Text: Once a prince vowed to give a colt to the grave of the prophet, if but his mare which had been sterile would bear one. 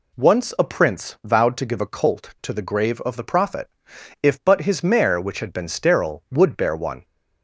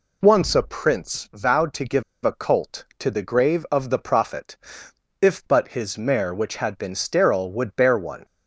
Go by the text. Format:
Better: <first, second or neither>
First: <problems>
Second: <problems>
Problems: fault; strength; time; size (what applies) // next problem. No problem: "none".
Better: first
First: none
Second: pauses between "give" and "a"; slight; at 2.0 s; 0.21 s long